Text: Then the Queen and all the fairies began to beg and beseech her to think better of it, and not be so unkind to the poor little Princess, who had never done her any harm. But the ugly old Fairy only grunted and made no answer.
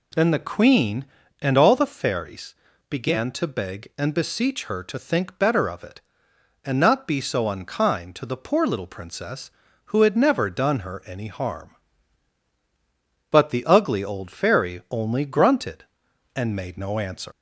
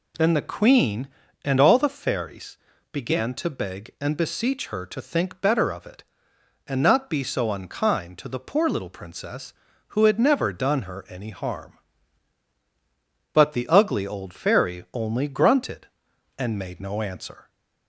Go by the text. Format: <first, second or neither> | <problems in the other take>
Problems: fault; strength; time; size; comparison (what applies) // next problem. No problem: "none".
second | pauses between "fairies" and "began"; slight; at 2.5 s; 0.34 s long; slight in the second // leaves "answer" unfinished; at 17.3 s; 150 ms